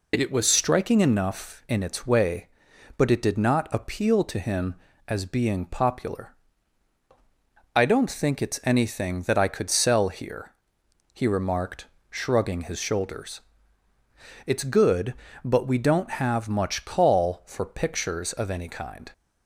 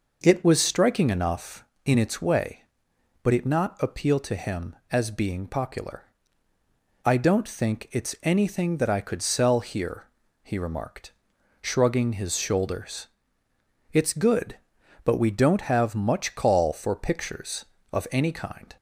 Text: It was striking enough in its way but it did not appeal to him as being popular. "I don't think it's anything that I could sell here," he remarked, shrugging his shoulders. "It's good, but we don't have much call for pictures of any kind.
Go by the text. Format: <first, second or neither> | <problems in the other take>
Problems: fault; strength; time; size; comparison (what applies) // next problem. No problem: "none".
first | skips "did"; at 3.4 s